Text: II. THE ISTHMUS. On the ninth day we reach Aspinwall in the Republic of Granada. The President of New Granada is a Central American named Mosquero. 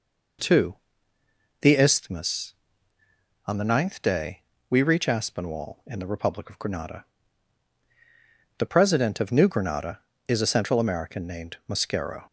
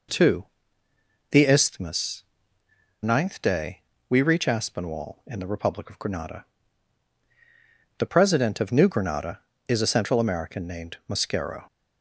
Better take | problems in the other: first | skips "On the"; at 2.6 s // pauses between "day" and "we"; slight; at 3.7 s; 0.30 s long; slight in the first

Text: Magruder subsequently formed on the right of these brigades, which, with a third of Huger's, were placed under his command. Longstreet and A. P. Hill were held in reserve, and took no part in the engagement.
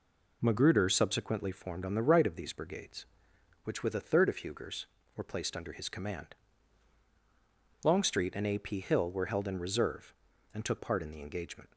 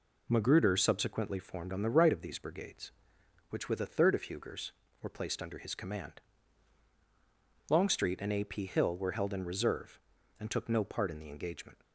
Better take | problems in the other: second | skips "no"; at 10.7 s

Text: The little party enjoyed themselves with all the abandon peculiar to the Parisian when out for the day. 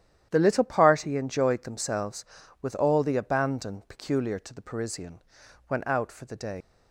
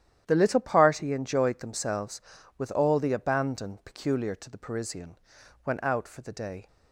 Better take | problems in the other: second | starts louder than the rest; strong; until 1.3 s; 11 dB; strong in the second // pauses between "Parisian" and "when"; noticeable; at 5.2 s; 0.48 s long; noticeable in the second // leaves "day" unfinished; at 6.6 s; 100 ms

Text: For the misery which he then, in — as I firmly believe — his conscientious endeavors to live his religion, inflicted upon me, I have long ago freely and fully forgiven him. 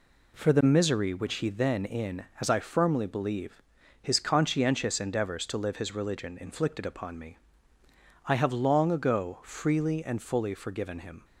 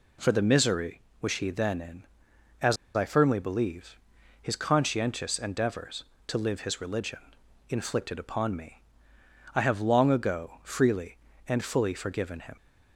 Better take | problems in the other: first | pauses between "as" and "I"; slight; at 2.7 s; 0.19 s long

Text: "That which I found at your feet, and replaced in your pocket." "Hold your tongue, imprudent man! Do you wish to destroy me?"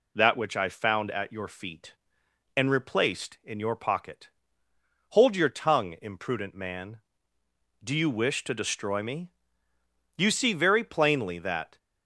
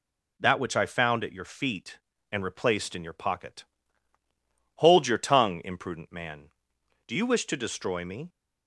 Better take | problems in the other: second | goes on to say "You see very plainly that"; from 10.1 s on; 1.6 s long

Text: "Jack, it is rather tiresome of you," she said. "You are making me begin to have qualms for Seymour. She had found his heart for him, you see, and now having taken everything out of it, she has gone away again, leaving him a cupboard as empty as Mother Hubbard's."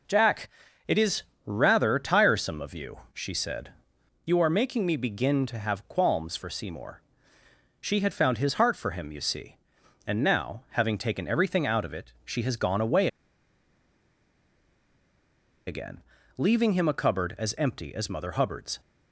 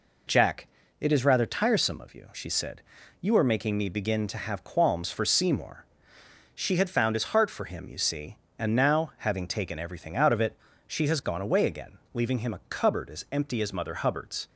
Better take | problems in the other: second | pauses between "is" and "rather"; slight; at 1.2 s; 0.24 s long // pauses between "away" and "again"; strong; at 13.0 s; 2.6 s long

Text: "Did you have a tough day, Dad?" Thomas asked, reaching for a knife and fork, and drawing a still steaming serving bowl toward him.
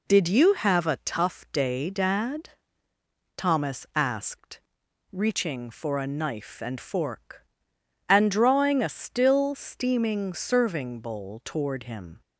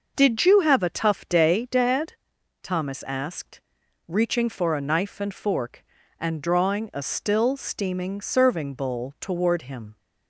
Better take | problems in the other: neither | none

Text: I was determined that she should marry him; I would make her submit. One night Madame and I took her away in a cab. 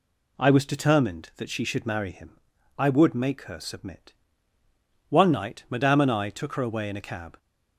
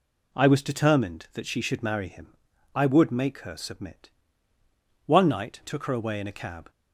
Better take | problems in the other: first | skips "Madame and I"; at 5.6 s

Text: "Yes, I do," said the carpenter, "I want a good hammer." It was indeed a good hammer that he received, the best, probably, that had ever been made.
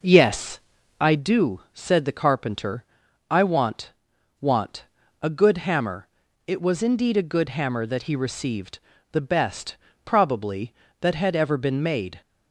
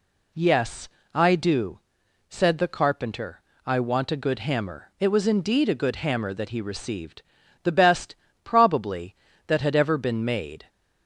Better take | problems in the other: second | says "want" twice; at 4.4 s

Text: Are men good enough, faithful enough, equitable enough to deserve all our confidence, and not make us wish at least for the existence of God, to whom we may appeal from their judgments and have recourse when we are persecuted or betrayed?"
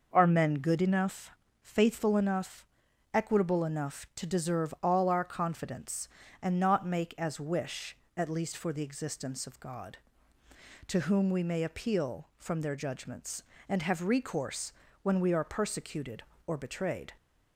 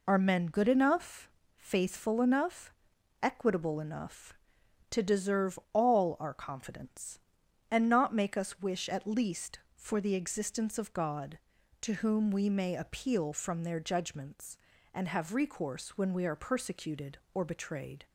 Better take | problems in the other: second | says "as" for "us"; at 7.1 s // pauses between "recourse" and "when"; slight; at 14.7 s; 0.30 s long

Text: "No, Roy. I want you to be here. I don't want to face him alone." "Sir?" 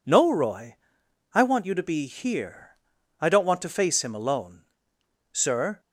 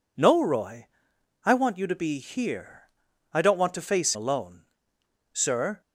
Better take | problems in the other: first | skips "him"; at 4.1 s

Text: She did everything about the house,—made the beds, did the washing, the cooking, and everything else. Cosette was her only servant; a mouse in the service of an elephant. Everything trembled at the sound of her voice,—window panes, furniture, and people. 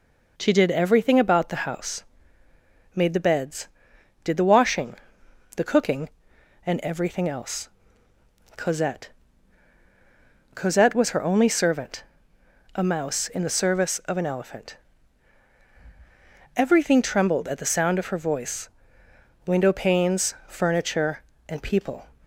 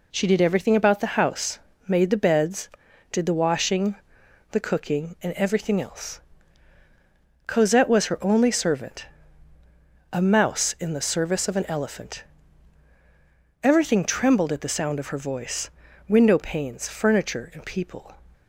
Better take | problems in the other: second | says "Cosette" twice; at 10.5 s

